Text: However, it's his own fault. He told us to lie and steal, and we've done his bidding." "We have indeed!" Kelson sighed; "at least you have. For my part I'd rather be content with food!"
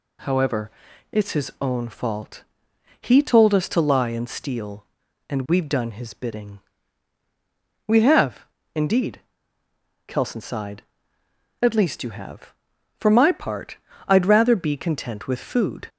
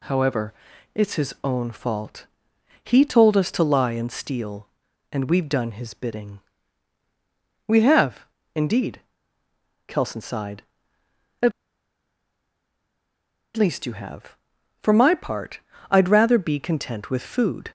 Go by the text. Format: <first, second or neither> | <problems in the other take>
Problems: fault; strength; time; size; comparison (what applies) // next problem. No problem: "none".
first | pauses between "have" and "indeed"; slight; at 8.2 s; 0.26 s long; slight in the first // pauses between "at" and "least"; strong; at 11.5 s; 2.0 s long // pauses between "part" and "I'd"; slight; at 15.6 s; 0.28 s long; slight in the first